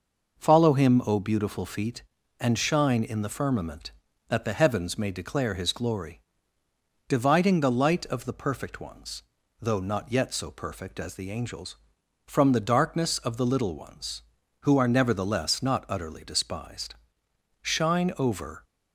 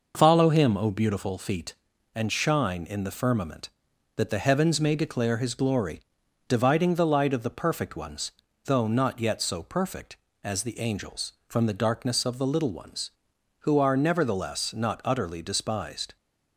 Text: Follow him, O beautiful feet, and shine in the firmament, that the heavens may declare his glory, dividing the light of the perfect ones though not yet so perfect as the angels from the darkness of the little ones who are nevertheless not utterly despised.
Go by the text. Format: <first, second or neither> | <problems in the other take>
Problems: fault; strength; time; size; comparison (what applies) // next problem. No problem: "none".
second | pauses between "ones" and "though"; slight; at 9.2 s; 0.36 s long; slight in the second // goes on to say "Shine over"; noticeable; from 17.6 s on; 1.0 s long